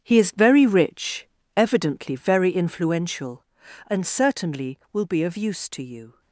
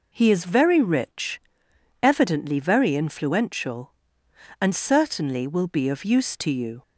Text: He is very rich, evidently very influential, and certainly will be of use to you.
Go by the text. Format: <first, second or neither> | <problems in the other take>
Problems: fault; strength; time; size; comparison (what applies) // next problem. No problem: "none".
second | gets quieter; strong; throughout; 11.5 dB